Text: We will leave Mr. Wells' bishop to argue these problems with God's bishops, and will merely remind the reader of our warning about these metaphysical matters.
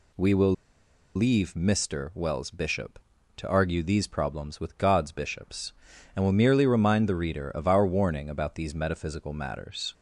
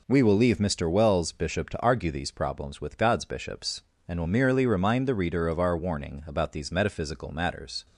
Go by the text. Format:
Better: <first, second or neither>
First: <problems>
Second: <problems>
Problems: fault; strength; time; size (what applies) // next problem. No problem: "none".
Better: second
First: pauses between "will" and "leave"; noticeable; at 0.5 s; 0.62 s long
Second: none